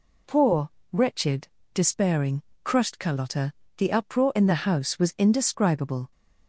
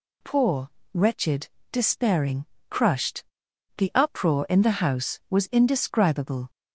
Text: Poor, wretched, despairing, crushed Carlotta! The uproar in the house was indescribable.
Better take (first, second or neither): first